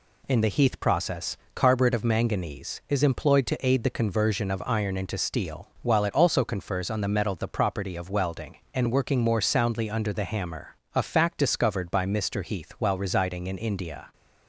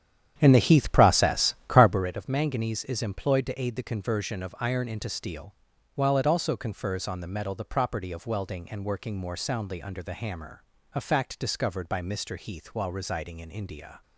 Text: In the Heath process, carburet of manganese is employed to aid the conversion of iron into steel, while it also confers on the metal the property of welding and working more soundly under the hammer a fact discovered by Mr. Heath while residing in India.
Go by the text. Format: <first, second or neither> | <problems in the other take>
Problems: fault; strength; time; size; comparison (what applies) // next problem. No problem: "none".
first | starts louder than the rest; strong; until 2.1 s; 9.5 dB // pauses between "hammer" and "a"; slight; at 10.6 s; 0.32 s long; slight in the first